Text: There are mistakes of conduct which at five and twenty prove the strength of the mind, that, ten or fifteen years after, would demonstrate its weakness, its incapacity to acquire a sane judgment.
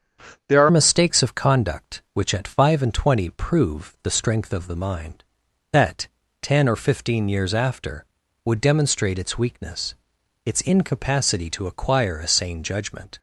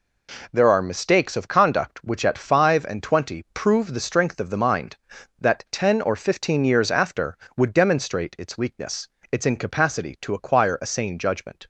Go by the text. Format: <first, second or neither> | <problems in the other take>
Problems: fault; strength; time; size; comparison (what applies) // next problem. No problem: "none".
second | starts louder than the rest; strong; until 1.5 s; 7 dB // changes voice at "mistakes"; from 0.7 s on; 12.4 s long